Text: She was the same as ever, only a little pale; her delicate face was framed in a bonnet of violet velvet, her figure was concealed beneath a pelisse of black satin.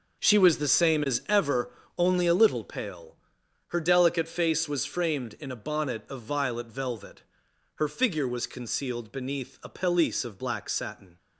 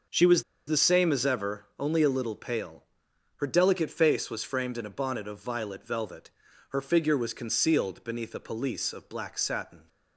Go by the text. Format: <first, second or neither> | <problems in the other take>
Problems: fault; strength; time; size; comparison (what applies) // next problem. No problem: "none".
first | pauses between "was" and "the"; slight; at 0.4 s; 0.24 s long